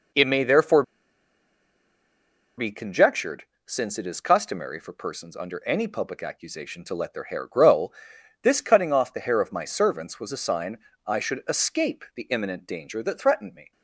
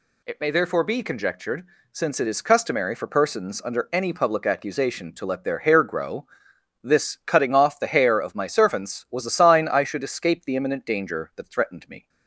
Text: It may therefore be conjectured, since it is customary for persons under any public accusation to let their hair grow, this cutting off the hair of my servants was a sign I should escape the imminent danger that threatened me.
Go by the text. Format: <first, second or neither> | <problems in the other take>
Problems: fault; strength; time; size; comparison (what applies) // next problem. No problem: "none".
second | pauses between "therefore" and "be"; strong; at 0.8 s; 1.7 s long // pauses between "sign" and "I"; slight; at 10.7 s; 0.28 s long